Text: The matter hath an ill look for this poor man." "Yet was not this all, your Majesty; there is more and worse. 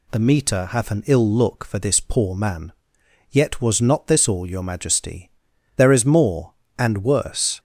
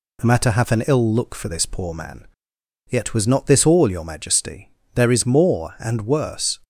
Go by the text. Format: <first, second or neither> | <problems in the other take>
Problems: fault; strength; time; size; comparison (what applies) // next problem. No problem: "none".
second | says "meter" for "matter"; at 0.1 s